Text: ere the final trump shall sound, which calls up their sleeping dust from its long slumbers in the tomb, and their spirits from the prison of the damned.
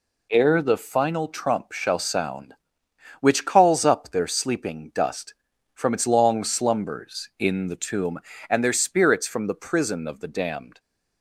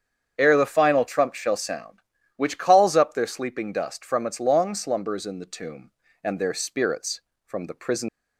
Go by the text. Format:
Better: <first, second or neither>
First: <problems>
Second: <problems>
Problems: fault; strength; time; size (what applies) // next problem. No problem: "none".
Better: first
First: none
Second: starts louder than the rest; strong; until 1.4 s; 7.5 dB // stops before "of the damned"; at 8.0 s